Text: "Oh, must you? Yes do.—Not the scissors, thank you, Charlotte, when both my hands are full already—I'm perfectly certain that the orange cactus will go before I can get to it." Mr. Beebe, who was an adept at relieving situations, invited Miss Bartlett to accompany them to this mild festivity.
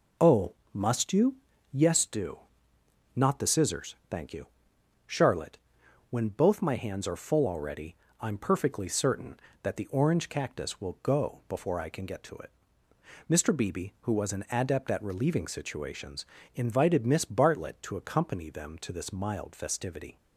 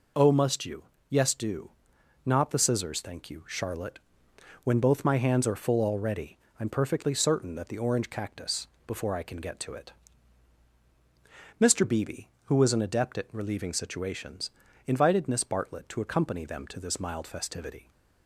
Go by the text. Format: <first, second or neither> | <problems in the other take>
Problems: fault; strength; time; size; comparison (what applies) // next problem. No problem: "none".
first | skips "will go"; at 8.7 s